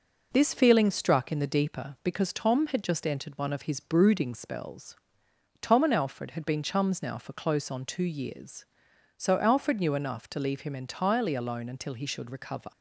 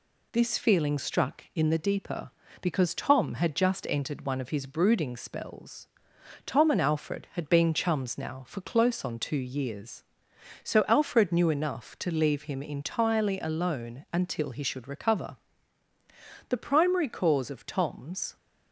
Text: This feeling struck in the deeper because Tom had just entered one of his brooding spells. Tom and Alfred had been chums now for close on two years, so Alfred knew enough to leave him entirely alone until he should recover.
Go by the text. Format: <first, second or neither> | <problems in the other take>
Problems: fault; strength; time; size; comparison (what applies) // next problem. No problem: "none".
first | goes on to say "The primary cause of Tom's"; strong; from 16.4 s on; 1.8 s long